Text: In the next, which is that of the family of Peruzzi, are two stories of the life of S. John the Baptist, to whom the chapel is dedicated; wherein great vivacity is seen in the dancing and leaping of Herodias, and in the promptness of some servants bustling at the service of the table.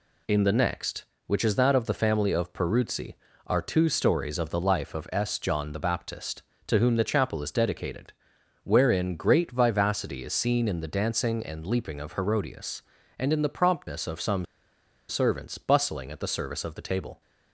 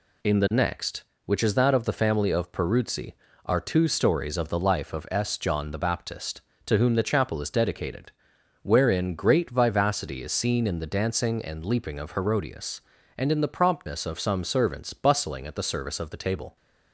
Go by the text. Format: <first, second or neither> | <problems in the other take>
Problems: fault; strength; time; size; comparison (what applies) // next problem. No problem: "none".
second | pauses between "some" and "servants"; noticeable; at 14.4 s; 0.64 s long